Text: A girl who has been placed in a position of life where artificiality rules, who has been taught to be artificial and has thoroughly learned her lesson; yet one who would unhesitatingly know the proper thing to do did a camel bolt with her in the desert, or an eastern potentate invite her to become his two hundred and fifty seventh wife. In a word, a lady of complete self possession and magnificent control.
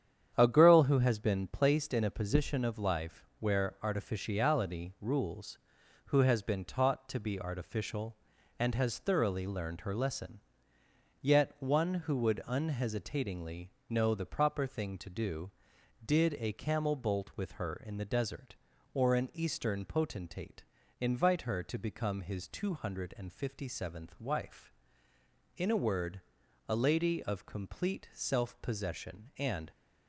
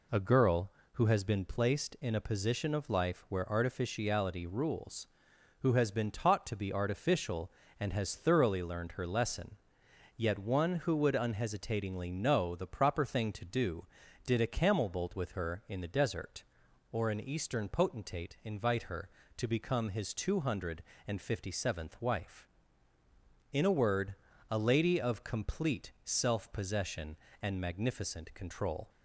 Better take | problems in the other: second | starts louder than the rest; strong; until 1.3 s; 9 dB // pauses between "unhesitatingly" and "know"; slight; at 13.6 s; 0.18 s long // pauses between "potentate" and "invite"; slight; at 20.6 s; 0.36 s long // stops before "magnificent control"; at 29.7 s

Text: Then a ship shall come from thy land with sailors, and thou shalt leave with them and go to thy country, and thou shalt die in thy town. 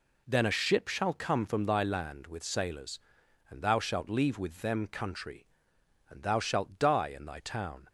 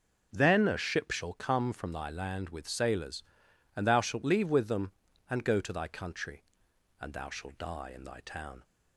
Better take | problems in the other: second | skips "and go to thy"; at 4.8 s

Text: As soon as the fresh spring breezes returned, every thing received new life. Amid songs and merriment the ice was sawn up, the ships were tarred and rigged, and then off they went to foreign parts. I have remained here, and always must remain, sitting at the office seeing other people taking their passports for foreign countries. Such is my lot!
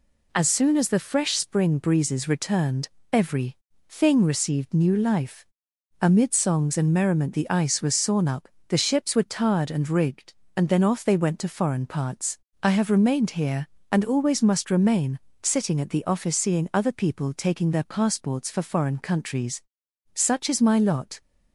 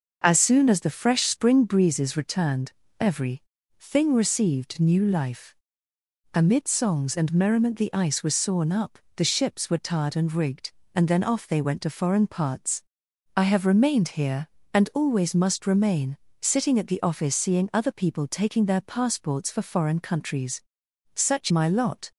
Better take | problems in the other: first | pauses between "every" and "thing"; at 3.4 s; 0.38 s long; slight in the first // skips "is"; at 21.5 s

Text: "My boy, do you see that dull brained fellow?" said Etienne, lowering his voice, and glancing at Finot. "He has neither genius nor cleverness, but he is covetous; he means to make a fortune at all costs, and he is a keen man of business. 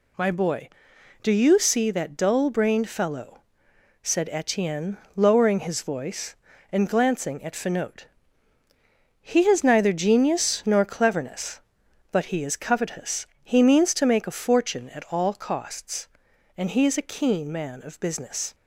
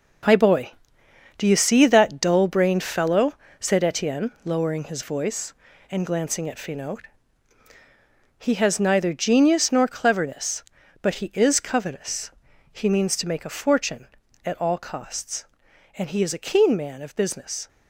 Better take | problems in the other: first | gets quieter; strong; throughout; 8.5 dB

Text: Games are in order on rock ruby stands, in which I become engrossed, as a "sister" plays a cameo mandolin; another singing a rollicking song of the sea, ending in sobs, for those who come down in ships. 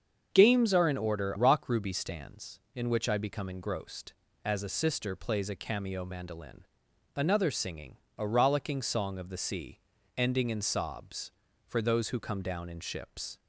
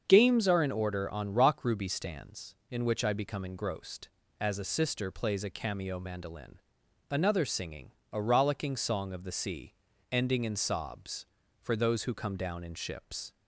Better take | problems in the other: second | starts louder than the rest; until 1.3 s; 7 dB; also in the second // skips "on"; at 1.3 s // pauses between "singing" and "a"; slight; at 7.9 s; 0.18 s long; slight in the second

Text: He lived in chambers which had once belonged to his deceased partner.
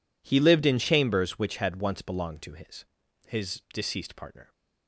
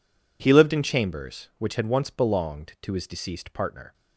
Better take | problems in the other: second | says "his" twice; at 3.2 s

